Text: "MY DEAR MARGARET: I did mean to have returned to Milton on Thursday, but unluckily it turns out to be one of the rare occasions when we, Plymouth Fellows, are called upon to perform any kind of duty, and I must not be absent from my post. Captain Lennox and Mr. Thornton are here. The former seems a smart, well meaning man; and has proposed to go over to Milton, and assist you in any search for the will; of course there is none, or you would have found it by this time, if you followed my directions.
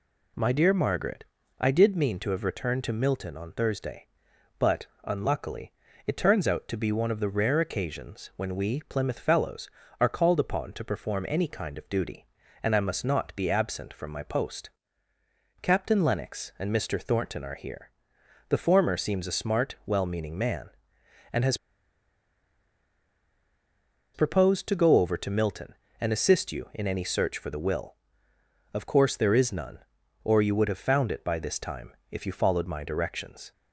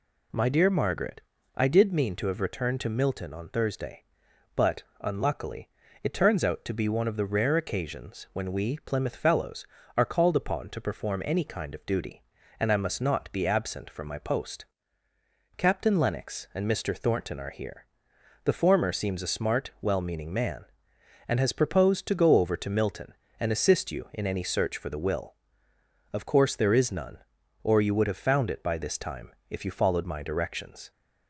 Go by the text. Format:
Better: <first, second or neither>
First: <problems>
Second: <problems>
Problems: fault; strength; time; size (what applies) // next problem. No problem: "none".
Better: second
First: pauses between "but" and "unluckily"; slight; at 4.8 s; 0.16 s long // pauses between "unluckily" and "it"; slight; at 5.7 s; 0.36 s long // pauses between "has" and "proposed"; strong; at 21.5 s; 2.5 s long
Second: pauses between "but" and "unluckily"; slight; at 4.8 s; 0.16 s long // pauses between "unluckily" and "it"; slight; at 5.6 s; 0.36 s long